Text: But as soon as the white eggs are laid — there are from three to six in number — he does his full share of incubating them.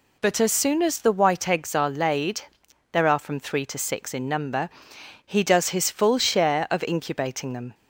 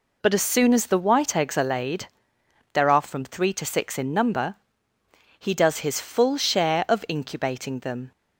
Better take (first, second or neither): neither